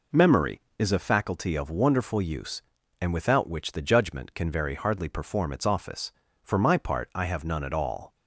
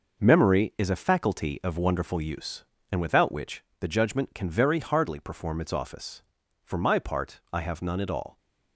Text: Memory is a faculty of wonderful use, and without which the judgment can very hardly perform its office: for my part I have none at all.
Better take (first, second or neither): first